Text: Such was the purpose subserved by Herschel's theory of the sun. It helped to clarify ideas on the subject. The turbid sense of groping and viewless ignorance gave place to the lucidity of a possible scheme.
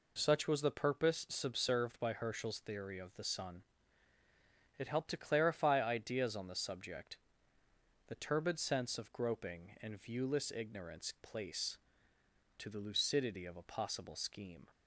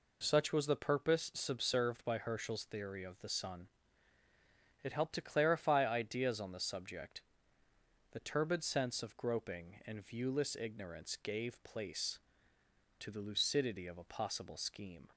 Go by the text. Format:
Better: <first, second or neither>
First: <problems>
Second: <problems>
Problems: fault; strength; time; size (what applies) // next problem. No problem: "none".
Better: second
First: skips "gave"; at 11.1 s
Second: none